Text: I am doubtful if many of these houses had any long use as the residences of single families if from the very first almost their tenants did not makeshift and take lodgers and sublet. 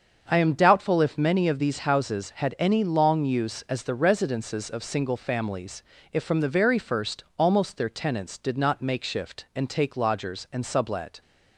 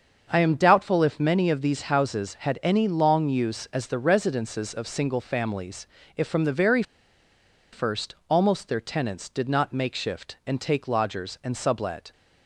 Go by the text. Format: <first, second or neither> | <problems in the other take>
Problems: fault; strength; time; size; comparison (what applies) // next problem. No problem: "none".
first | starts louder than the rest; until 1.3 s; 6.5 dB; also in the first // pauses between "families" and "if"; slight; at 5.8 s; 0.30 s long; slight in the first // pauses between "very" and "first"; noticeable; at 6.8 s; 0.90 s long